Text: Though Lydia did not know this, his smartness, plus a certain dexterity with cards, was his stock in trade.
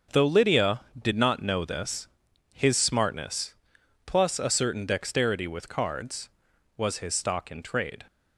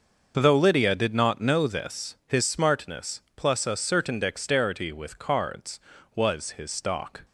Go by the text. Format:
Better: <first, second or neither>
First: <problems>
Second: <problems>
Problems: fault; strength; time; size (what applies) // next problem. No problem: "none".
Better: first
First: starts louder than the rest; until 1.3 s; 6.5 dB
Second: starts louder than the rest; noticeable; until 1.4 s; 6 dB // stops before "in trade"; at 7.2 s